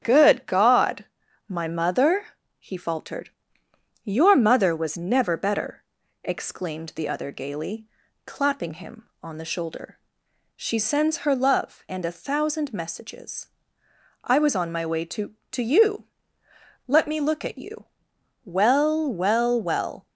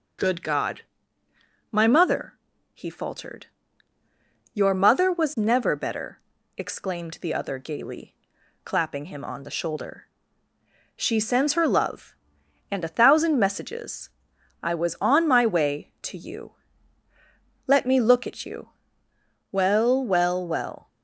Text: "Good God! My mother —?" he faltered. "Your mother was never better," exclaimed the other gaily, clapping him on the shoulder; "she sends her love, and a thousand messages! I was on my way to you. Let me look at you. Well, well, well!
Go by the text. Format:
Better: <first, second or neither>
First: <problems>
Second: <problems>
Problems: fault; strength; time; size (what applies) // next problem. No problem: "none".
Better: second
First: starts louder than the rest; strong; until 1.0 s; 9 dB // says "to" twice; at 15.5 s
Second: starts louder than the rest; noticeable; until 2.1 s; 6 dB